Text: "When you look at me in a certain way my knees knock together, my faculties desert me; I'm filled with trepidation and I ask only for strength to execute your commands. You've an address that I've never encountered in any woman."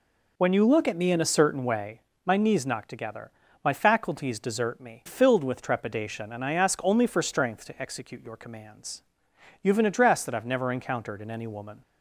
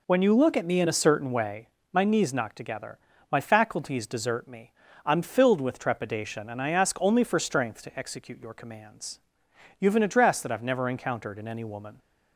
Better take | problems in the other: second | pauses between "way" and "my"; slight; at 2.0 s; 0.24 s long; slight in the second // skips "I'm"; at 5.0 s

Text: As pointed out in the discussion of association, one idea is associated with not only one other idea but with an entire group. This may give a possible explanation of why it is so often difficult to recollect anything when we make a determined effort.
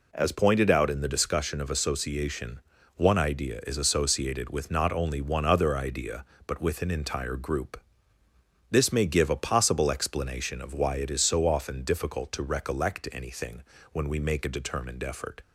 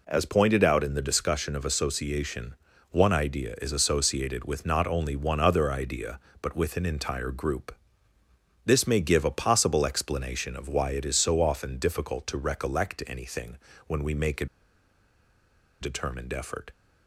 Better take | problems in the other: first | pauses between "anything" and "when"; slight; at 13.5 s; 0.30 s long; slight in the first // pauses between "a" and "determined"; strong; at 14.4 s; 1.3 s long

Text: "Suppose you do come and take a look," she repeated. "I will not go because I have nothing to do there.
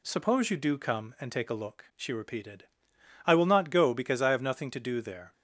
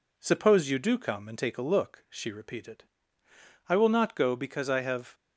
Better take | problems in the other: first | stops before "nothing to do there"; at 5.1 s

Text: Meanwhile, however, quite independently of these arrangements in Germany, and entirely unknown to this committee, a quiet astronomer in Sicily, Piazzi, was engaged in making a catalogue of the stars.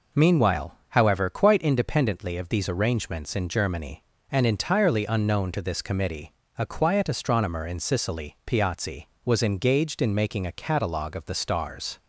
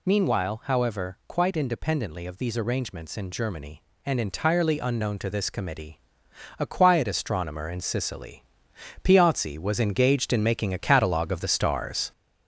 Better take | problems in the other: first | gets louder; noticeable; throughout; 4.5 dB

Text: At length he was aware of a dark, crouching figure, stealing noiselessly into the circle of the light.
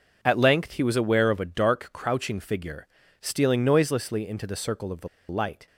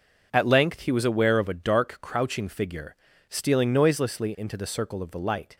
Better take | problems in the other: second | pauses between "the" and "light"; slight; at 5.0 s; 0.22 s long

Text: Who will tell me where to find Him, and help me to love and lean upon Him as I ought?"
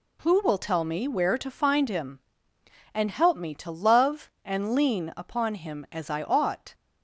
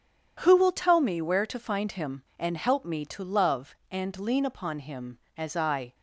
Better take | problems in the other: first | stops before "ought"; at 5.9 s

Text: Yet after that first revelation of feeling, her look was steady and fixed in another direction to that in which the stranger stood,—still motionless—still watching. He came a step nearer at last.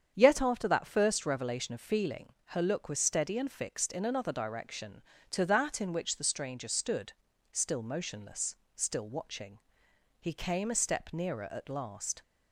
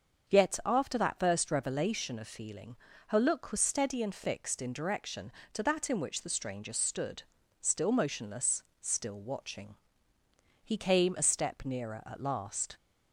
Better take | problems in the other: first | starts louder than the rest; until 1.3 s; 7 dB; strong in the first // skips "another"; at 4.7 s

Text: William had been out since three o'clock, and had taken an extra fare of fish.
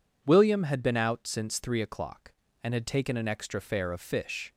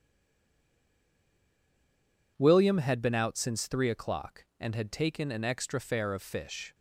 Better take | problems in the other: first | stays silent before the first word; until 2.3 s; 2.3 s long

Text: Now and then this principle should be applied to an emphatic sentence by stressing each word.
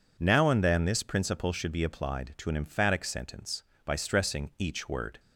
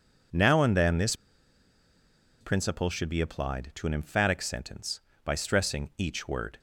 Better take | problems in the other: first | pauses between "this" and "principle"; at 1.1 s; 1.2 s long

